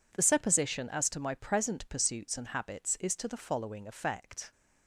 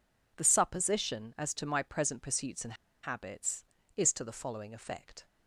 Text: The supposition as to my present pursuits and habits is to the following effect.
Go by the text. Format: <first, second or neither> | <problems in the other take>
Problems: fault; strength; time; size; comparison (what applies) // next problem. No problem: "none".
first | pauses between "and" and "habits"; slight; at 2.7 s; 0.29 s long